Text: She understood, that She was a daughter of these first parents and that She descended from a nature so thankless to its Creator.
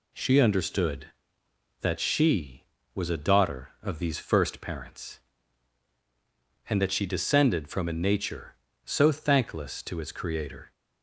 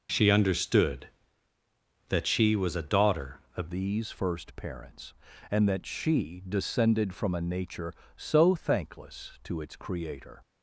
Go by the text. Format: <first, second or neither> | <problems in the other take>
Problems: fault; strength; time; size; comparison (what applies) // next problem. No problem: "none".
first | changes voice at "these"; from 3.6 s on; 6.8 s long